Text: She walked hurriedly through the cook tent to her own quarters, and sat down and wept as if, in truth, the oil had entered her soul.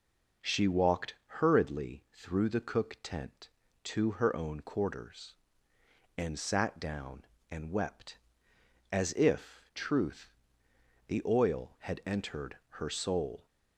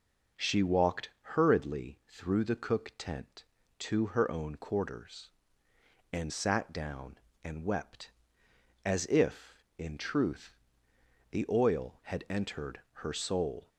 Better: second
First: pauses between "walked" and "hurriedly"; slight; at 1.1 s; 0.24 s long // skips "in"; at 9.6 s // pauses between "entered" and "her"; slight; at 12.5 s; 0.24 s long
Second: pauses between "walked" and "hurriedly"; slight; at 1.1 s; 0.24 s long // pauses between "entered" and "her"; slight; at 12.8 s; 0.24 s long

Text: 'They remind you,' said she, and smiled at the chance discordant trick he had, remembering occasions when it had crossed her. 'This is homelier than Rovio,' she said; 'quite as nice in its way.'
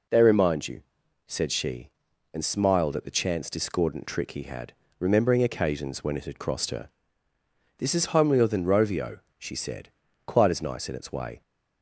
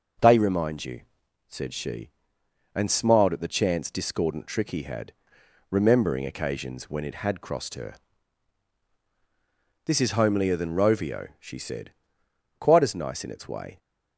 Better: neither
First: none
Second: none

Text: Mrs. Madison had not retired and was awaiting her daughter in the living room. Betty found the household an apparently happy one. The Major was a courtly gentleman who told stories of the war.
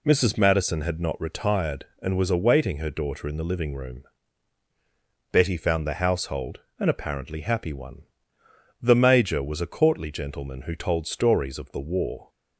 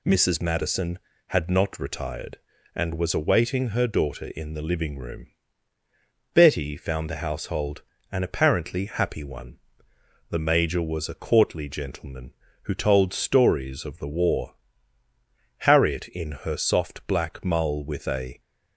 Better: first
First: pauses between "household" and "an"; slight; at 6.5 s; 0.20 s long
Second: pauses between "household" and "an"; slight; at 7.8 s; 0.30 s long // goes on to say "Harriet in her soft black mull with a"; strong; from 15.6 s on; 2.7 s long

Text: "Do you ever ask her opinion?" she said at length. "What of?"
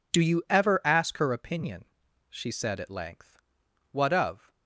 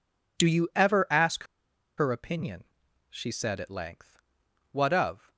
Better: first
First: none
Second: pauses between "ask" and "her"; noticeable; at 1.4 s; 0.52 s long

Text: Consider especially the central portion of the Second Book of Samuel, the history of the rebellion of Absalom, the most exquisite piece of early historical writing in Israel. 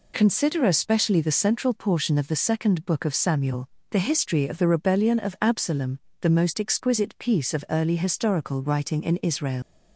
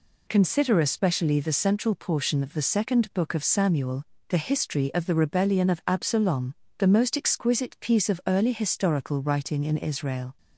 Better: second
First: leaves "Israel" unfinished; at 9.6 s; 125 ms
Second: none

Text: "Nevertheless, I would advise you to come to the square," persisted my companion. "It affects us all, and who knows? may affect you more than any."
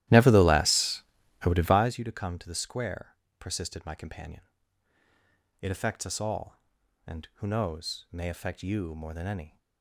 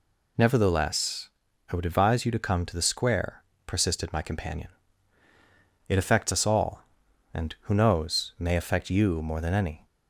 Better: second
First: starts louder than the rest; strong; until 2.0 s; 14 dB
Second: none

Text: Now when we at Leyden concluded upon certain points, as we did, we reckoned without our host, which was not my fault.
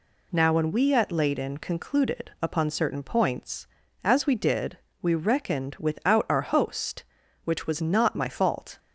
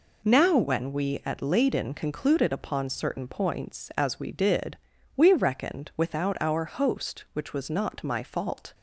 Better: neither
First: none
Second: none

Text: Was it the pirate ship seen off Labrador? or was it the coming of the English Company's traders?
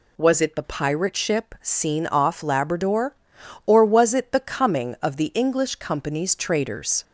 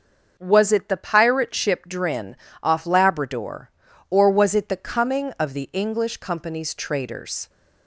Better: first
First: none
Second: starts louder than the rest; noticeable; until 1.3 s; 6 dB // says "drin" for "seen"; at 1.8 s

